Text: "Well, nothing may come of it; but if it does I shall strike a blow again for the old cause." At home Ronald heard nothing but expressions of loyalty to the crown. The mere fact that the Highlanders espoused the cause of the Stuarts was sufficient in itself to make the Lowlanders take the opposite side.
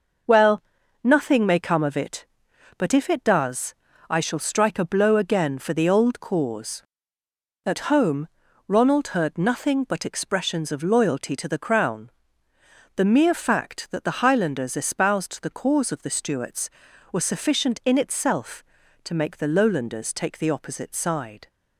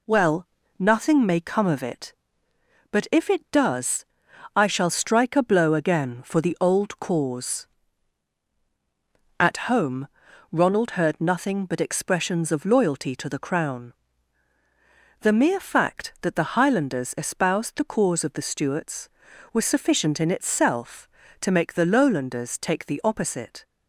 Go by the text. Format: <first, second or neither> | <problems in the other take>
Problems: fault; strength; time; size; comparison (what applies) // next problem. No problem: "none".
first | pauses between "does" and "I"; noticeable; at 4.0 s; 0.50 s long; slight in the first // pauses between "home" and "Ronald"; at 10.0 s; 0.44 s long; also in the first // stops before "side"; at 23.6 s